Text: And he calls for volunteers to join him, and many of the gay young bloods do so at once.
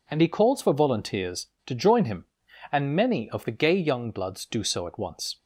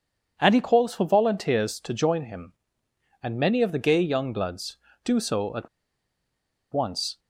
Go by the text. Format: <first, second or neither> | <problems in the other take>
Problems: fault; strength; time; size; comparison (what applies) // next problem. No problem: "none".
first | pauses between "at" and "once"; at 5.6 s; 1.0 s long